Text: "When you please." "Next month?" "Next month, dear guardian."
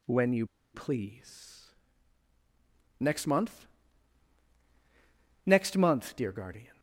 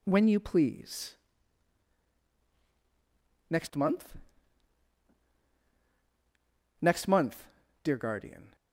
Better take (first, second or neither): second